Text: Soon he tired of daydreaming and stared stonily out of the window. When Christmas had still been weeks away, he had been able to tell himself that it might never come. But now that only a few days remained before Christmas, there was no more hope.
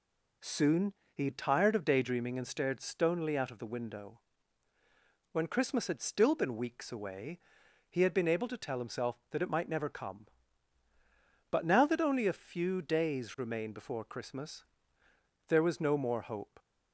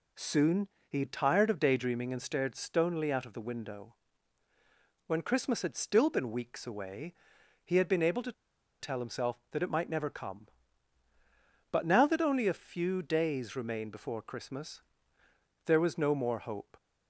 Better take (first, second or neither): first